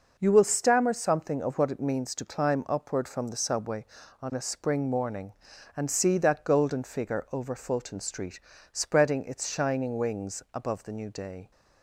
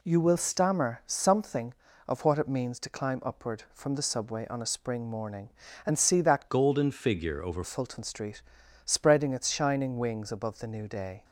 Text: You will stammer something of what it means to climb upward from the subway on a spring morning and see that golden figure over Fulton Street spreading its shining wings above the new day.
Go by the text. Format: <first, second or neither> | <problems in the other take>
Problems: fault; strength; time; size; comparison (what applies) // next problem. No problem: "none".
first | changes voice from "golden" to "over"; from 6.4 to 7.6 s; 1.2 s long // pauses between "Street" and "spreading"; at 8.4 s; 0.42 s long; slight in the first